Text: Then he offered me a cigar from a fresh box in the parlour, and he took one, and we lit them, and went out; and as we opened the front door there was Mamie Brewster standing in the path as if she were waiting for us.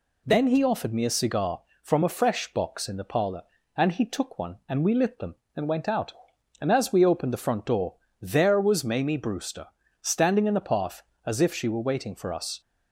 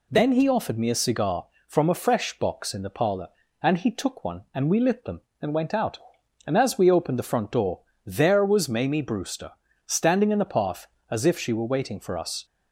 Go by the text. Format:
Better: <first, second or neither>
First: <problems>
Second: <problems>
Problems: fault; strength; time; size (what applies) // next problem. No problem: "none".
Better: neither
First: pauses between "door" and "there"; slight; at 7.9 s; 0.26 s long // pauses between "Brewster" and "standing"; slight; at 9.6 s; 0.34 s long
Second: pauses between "door" and "there"; slight; at 7.8 s; 0.25 s long // pauses between "Brewster" and "standing"; slight; at 9.5 s; 0.34 s long